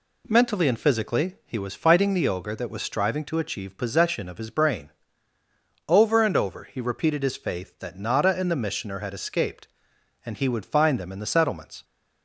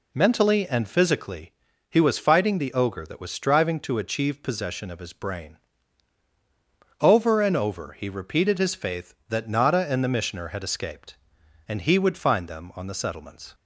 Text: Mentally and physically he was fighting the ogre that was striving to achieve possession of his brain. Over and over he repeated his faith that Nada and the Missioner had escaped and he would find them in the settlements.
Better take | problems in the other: first | pauses between "physically" and "he"; slight; at 1.5 s; 0.36 s long // says "on" for "in"; at 12.7 s

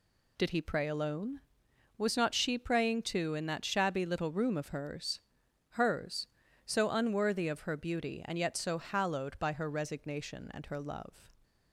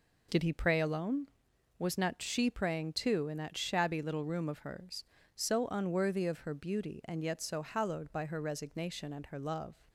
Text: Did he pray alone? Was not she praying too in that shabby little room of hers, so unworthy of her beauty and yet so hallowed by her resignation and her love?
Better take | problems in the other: second | says "hers" twice; at 5.6 s

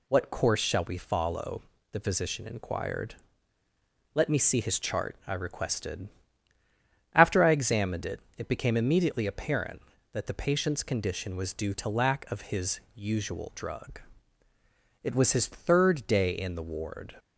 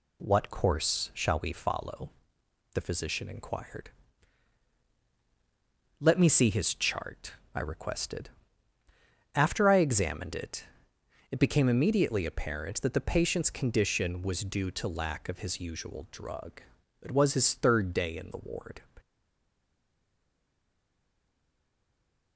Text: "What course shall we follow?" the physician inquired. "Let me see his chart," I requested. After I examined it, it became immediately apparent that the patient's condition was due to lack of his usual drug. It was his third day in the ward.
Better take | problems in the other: first | stays silent after the last word; strong; from 18.9 s on; 3.4 s long

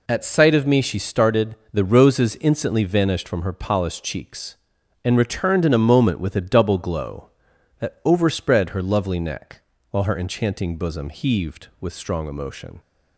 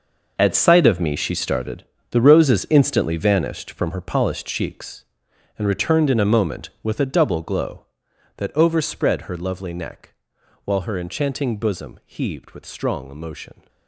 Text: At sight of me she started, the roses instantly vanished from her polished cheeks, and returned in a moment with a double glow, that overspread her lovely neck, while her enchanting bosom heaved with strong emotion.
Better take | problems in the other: first | gets quieter; strong; throughout; 12.5 dB

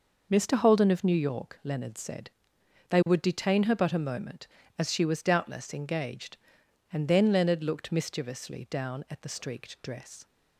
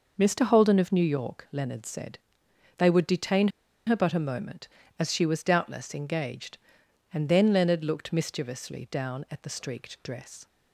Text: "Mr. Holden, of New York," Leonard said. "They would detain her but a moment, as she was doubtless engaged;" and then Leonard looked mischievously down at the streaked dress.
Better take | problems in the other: first | pauses between "detain" and "her"; at 3.4 s; 0.38 s long

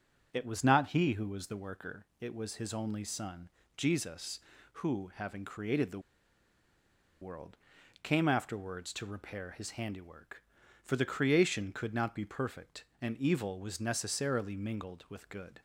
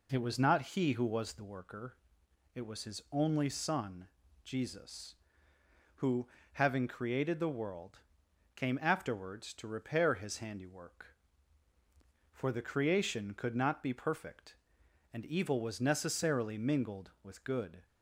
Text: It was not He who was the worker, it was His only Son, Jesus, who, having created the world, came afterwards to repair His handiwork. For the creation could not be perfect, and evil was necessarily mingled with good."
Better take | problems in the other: second | starts louder than the rest; until 1.3 s; 7 dB // pauses between "the" and "world"; at 5.9 s; 1.2 s long

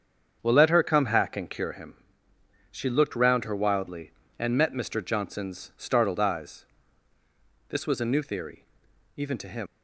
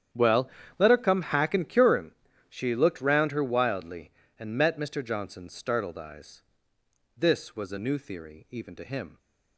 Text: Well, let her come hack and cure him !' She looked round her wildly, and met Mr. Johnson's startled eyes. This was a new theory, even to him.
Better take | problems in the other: second | starts louder than the rest; strong; until 1.4 s; 7.5 dB; strong in the second // leaves "him" unfinished; at 9.6 s; 115 ms

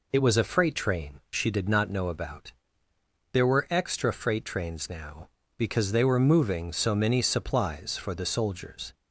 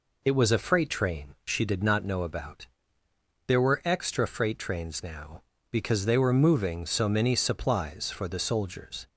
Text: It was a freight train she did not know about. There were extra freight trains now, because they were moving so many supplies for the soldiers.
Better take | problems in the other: neither | none

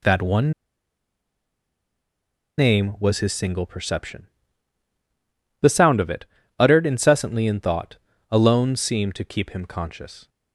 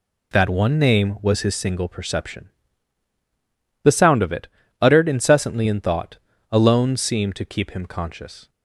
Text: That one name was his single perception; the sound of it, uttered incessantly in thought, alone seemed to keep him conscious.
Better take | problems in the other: second | pauses between "one" and "name"; strong; at 0.5 s; 2.0 s long

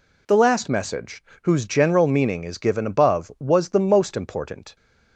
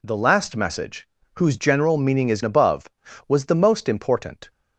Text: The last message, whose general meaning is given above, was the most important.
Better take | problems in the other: first | skips "given"; at 2.4 s

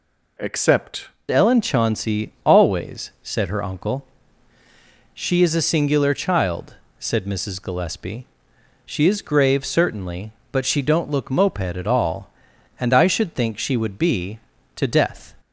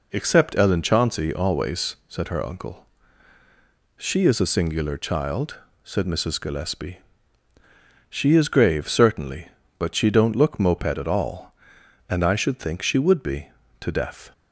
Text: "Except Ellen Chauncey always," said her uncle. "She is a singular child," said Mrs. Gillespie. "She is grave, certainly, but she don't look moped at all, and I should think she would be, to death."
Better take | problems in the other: second | changes voice at "Ellen"; from 1.3 s on; 14.0 s long

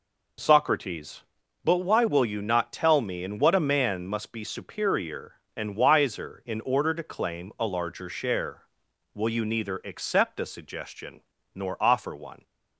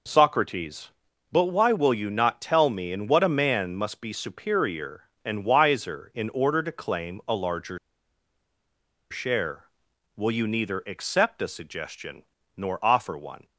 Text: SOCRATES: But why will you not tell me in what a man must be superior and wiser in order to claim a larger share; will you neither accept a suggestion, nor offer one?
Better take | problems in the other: first | pauses between "larger" and "share"; strong; at 7.7 s; 1.3 s long

